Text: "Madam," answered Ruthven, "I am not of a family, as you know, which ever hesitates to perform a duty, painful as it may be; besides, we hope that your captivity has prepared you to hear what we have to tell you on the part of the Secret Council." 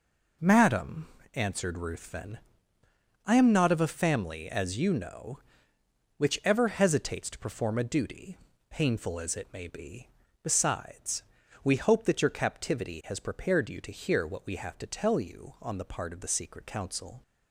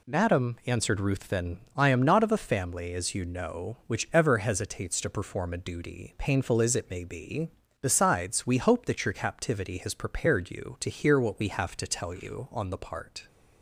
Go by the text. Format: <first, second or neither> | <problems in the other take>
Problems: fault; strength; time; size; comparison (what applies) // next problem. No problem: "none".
first | stops before "of the Secret Council"; at 13.2 s